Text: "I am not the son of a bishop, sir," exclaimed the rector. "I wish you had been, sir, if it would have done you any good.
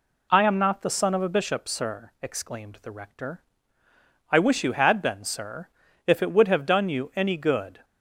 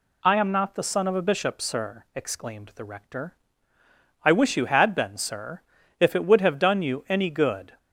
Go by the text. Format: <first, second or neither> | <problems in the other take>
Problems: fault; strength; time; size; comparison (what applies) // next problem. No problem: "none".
second | starts louder than the rest; slight; until 1.3 s; 2.5 dB